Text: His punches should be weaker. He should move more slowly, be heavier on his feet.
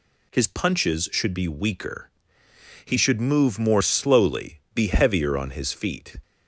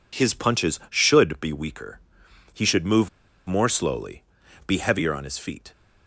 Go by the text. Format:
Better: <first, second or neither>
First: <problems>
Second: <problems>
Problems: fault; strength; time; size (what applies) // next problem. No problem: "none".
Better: first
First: none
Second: pauses between "move" and "more"; at 3.0 s; 0.38 s long